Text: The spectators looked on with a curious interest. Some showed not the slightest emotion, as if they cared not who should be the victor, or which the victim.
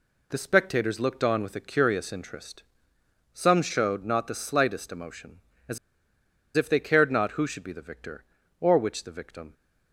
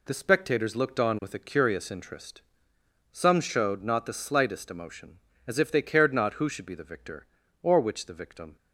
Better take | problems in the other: second | pauses between "as" and "if"; noticeable; at 5.7 s; 0.79 s long

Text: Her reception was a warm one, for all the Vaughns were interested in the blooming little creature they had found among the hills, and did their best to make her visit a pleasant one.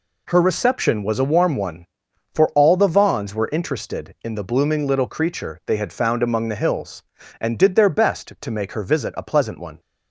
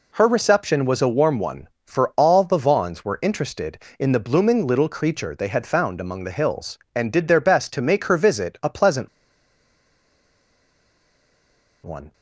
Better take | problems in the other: first | pauses between "pleasant" and "one"; strong; at 9.0 s; 2.7 s long

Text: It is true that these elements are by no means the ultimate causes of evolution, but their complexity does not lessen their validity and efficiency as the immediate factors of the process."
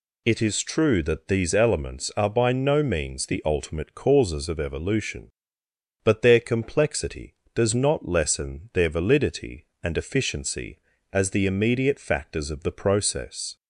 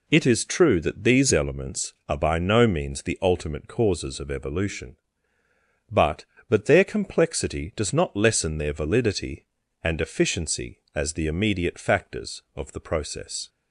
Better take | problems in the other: first | says "but" twice; at 6.4 s

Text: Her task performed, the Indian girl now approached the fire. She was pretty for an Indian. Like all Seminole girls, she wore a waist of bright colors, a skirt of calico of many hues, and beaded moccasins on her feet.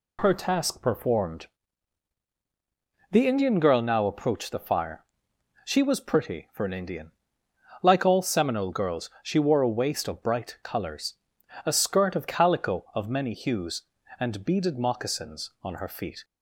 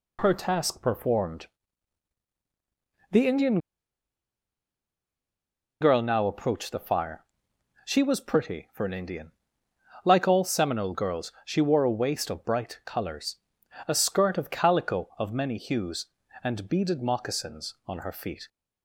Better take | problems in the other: first | pauses between "Indian" and "girl"; strong; at 3.5 s; 2.2 s long

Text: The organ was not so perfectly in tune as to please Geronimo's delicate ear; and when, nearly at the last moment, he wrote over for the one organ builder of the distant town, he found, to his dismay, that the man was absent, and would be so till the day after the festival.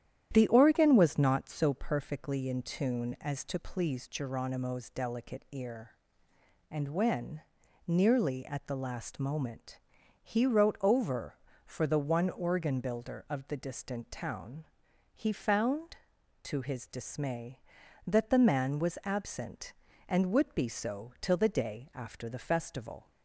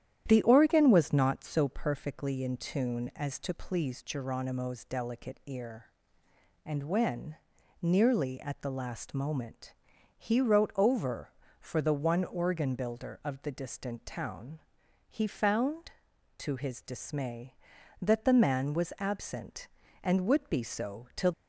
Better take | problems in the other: first | starts louder than the rest; strong; until 1.2 s; 10.5 dB; strong in the first // stops before "the day after the festival"; at 21.3 s

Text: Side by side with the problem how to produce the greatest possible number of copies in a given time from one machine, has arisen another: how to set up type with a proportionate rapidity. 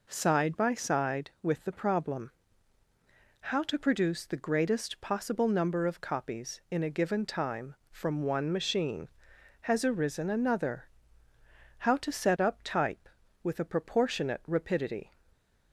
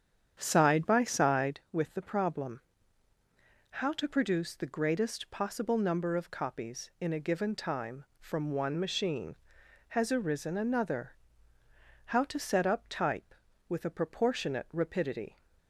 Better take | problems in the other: first | starts louder than the rest; strong; until 1.6 s; 8.5 dB // pauses between "problem" and "how"; at 2.6 s; 1.1 s long; also in the first

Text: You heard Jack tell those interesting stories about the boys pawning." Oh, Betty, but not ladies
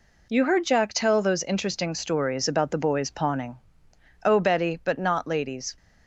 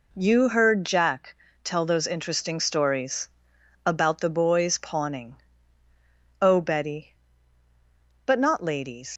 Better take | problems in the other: first | pauses between "Jack" and "tell"; slight; at 1.3 s; 0.30 s long // pauses between "stories" and "about"; noticeable; at 3.2 s; 0.56 s long // leaves "ladies" unfinished; at 9.1 s; 100 ms

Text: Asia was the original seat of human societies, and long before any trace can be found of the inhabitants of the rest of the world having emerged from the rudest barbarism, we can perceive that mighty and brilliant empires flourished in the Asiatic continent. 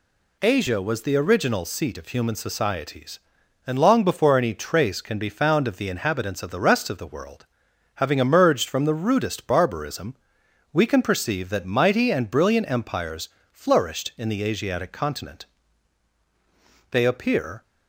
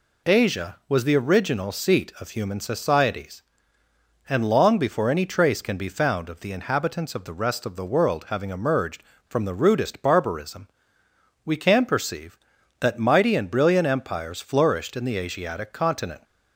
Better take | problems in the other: second | pauses between "world" and "having"; noticeable; at 7.4 s; 0.50 s long // pauses between "empires" and "flourished"; slight; at 13.3 s; 0.22 s long // goes on to say "They appear"; noticeable; from 16.9 s on; 0.72 s long

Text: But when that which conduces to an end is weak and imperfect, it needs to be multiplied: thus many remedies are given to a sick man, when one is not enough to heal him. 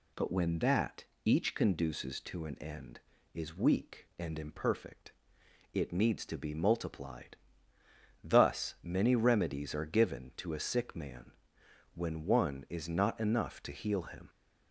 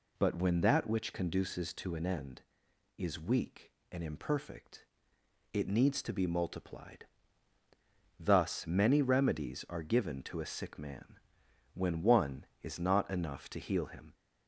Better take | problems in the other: second | says "each" for "which"; at 1.2 s

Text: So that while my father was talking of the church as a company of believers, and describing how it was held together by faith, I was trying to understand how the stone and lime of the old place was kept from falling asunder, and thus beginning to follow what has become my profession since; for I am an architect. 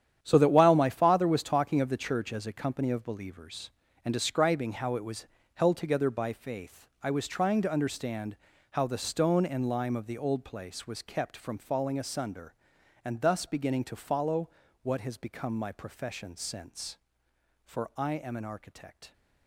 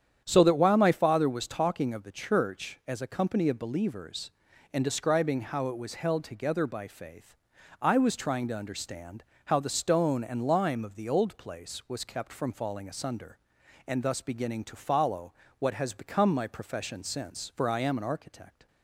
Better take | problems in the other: second | gets quieter; strong; throughout; 11.5 dB // starts louder than the rest; strong; until 1.2 s; 9.5 dB; strong in the second // pauses between "was" and "held"; slight; at 5.2 s; 0.28 s long // pauses between "understand" and "how"; slight; at 8.3 s; 0.34 s long; slight in the second // pauses between "follow" and "what"; slight; at 14.4 s; 0.34 s long; slight in the second

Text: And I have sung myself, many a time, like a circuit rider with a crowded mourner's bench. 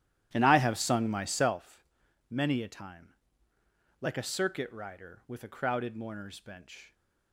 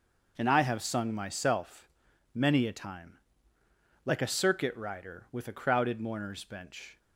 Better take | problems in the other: second | starts louder than the rest; strong; until 1.6 s; 12 dB

